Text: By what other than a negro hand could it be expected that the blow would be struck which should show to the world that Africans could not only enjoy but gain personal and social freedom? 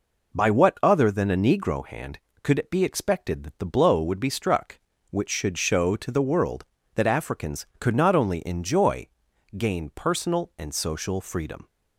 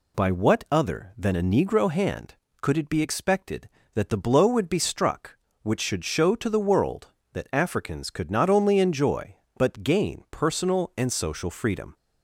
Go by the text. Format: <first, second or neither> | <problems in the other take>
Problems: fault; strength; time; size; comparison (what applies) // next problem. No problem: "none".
second | skips "but"; at 9.3 s